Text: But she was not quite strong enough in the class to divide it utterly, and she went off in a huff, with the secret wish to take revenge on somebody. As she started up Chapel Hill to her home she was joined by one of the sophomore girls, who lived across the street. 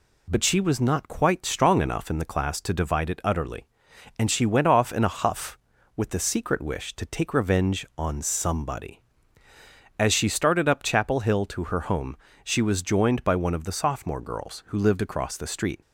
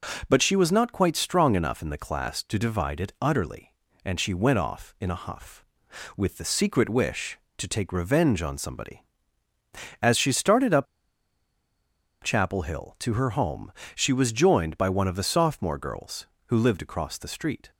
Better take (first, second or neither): first